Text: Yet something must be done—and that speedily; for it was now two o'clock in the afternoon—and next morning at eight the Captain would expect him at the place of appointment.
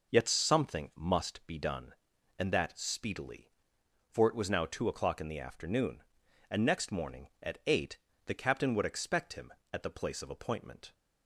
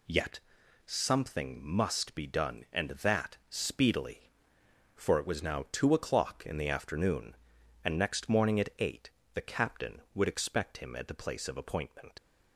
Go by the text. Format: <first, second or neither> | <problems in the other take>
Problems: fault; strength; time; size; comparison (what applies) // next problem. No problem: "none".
first | pauses between "Yet" and "something"; noticeable; at 0.3 s; 0.46 s long // pauses between "eight" and "the"; slight; at 9.1 s; 0.24 s long; slight in the first // leaves "appointment" unfinished; at 12.1 s; 45 ms